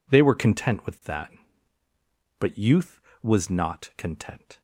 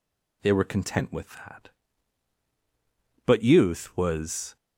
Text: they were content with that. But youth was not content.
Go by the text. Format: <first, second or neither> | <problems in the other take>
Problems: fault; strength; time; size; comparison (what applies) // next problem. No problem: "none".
first | stops before "not content"; at 4.5 s